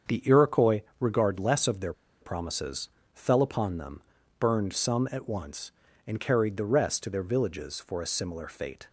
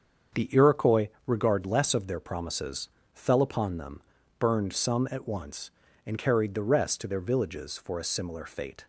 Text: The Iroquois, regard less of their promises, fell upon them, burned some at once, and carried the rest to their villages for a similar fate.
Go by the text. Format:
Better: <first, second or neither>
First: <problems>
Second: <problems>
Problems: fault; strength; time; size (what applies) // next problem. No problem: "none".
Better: second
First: starts louder than the rest; strong; until 1.2 s; 7 dB // pauses between "their" and "promises"; slight; at 1.9 s; 0.28 s long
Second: starts louder than the rest; strong; until 1.5 s; 7 dB